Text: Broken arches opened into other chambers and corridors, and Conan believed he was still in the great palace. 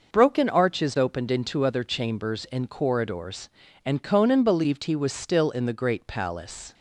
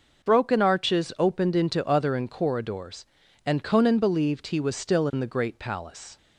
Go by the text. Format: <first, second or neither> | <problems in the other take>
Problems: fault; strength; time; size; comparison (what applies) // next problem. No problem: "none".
first | skips "chambers"; at 2.1 s